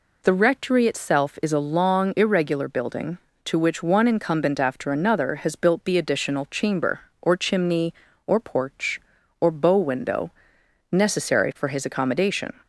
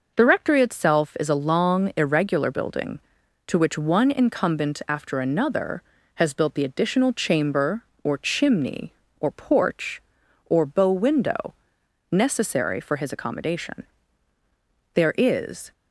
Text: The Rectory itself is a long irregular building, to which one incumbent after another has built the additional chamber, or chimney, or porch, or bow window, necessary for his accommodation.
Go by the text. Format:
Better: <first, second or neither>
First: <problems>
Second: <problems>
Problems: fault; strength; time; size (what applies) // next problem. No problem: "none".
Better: first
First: none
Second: goes on to say "There is"; noticeable; from 14.9 s on; 0.76 s long